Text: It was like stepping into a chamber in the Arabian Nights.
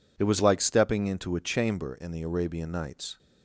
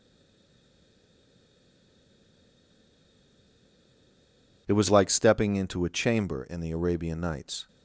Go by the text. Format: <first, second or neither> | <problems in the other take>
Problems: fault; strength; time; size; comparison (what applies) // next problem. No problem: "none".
first | stays silent before the first word; strong; until 4.6 s; 4.6 s long